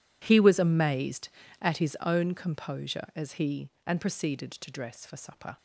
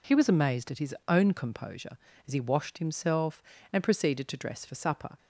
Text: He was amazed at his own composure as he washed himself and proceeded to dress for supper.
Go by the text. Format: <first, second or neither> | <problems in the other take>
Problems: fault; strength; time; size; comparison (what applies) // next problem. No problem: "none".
second | skips "washed himself"; at 3.7 s